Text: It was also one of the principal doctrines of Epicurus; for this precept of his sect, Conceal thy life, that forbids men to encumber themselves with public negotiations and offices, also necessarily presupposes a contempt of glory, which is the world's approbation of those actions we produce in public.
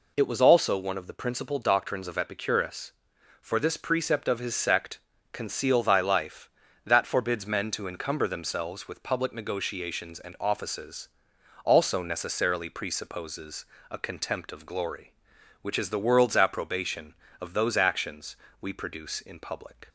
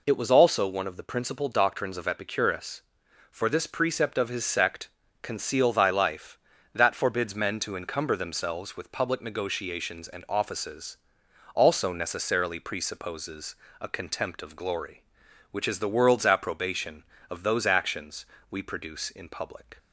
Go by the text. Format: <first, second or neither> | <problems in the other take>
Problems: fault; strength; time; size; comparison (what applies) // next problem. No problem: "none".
neither | pauses between "presupposes" and "a"; slight; the same in both // pauses between "actions" and "we"; slight; the same in both